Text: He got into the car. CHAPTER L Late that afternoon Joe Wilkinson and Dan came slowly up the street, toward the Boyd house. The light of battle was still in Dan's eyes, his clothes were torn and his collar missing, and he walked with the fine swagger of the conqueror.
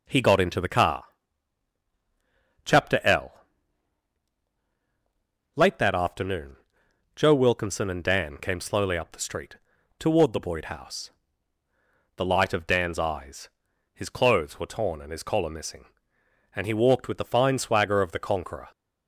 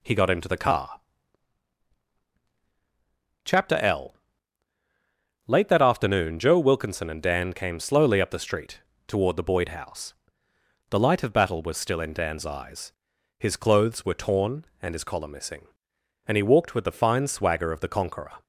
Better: second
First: pauses between "L" and "Late"; strong; at 3.3 s; 2.2 s long // pauses between "afternoon" and "Joe"; noticeable; at 6.5 s; 0.62 s long // skips "battle was still in"; at 12.6 s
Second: pauses between "L" and "Late"; strong; at 4.1 s; 1.3 s long

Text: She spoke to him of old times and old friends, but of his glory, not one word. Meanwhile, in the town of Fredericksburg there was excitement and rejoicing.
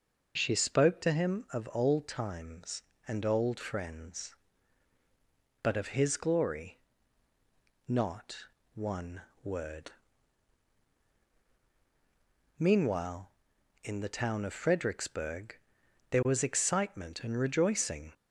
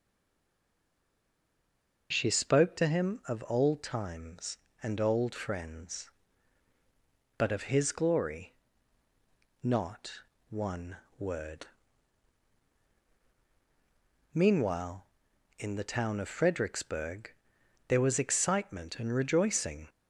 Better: first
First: pauses between "not" and "one"; slight; at 8.4 s; 0.30 s long // pauses between "one" and "word"; slight; at 9.2 s; 0.20 s long // pauses between "Fredericksburg" and "there"; noticeable; at 15.5 s; 0.54 s long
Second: stays silent before the first word; noticeable; until 2.1 s; 2.1 s long // pauses between "not" and "one"; slight; at 10.1 s; 0.30 s long // pauses between "one" and "word"; slight; at 10.9 s; 0.20 s long // pauses between "Fredericksburg" and "there"; noticeable; at 17.3 s; 0.56 s long

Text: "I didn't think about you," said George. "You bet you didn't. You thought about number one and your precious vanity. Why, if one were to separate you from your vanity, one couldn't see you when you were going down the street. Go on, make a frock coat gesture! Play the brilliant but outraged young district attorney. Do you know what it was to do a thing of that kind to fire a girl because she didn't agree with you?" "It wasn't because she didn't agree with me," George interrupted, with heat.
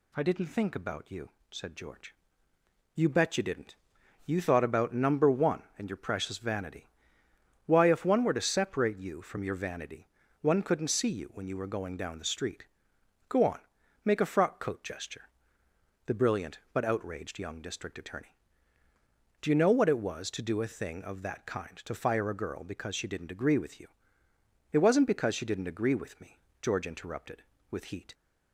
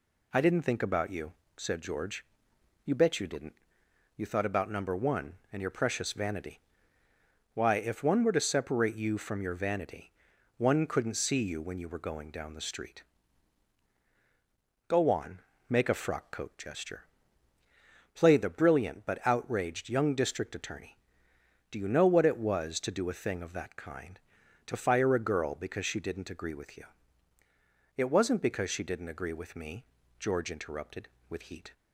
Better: second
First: skips "Play"; at 15.6 s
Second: none

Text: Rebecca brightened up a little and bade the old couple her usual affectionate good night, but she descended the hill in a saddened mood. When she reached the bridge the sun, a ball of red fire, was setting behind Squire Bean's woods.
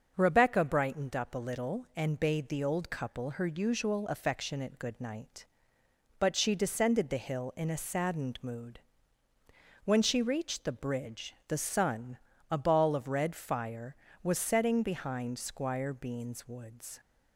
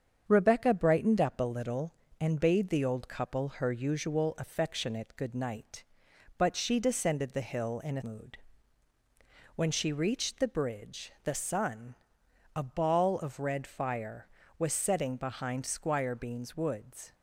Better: first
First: starts louder than the rest; until 1.1 s; 6.5 dB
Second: starts louder than the rest; strong; until 1.2 s; 7.5 dB // skips "saddened"; at 8.0 s

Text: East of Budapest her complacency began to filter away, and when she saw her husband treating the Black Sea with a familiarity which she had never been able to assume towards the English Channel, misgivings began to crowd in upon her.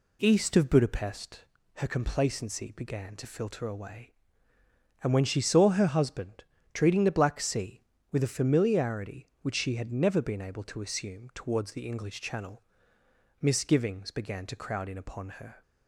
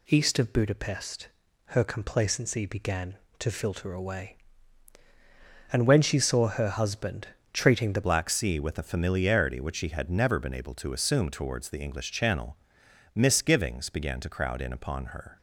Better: first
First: pauses between "Budapest" and "her"; slight; at 1.4 s; 0.32 s long // pauses between "husband" and "treating"; slight; at 6.4 s; 0.30 s long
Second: pauses between "Budapest" and "her"; at 1.2 s; 0.40 s long // pauses between "husband" and "treating"; slight; at 7.2 s; 0.26 s long // changes voice at "Black"; from 8.0 s on; 7.3 s long

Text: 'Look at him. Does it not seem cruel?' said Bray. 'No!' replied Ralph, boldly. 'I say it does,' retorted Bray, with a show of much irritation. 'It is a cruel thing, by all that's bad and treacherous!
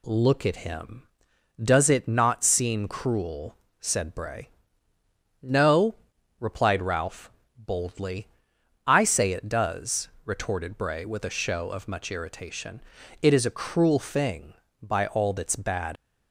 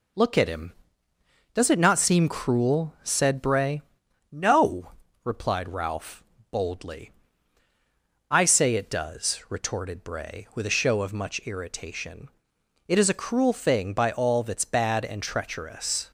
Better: second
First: stops before "and treacherous"; at 15.9 s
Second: none

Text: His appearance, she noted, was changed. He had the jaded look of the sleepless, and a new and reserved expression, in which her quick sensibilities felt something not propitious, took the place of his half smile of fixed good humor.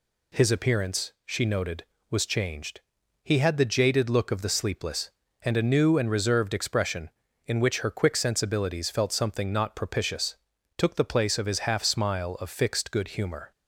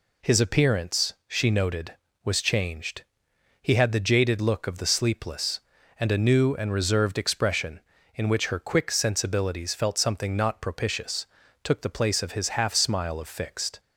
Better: first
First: none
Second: stops before "good humor"; at 13.7 s

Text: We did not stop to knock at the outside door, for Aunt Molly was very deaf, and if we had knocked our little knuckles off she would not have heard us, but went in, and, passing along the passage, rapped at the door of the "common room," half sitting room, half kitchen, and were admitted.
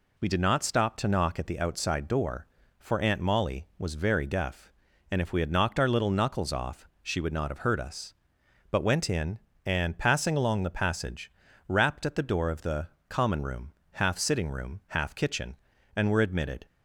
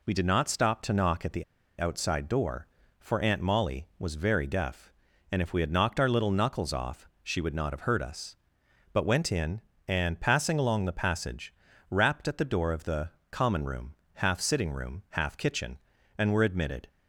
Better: first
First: pauses between "the" and "common"; slight; at 12.8 s; 0.22 s long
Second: pauses between "the" and "outside"; at 1.4 s; 0.36 s long // pauses between "the" and "common"; slight; at 13.0 s; 0.22 s long

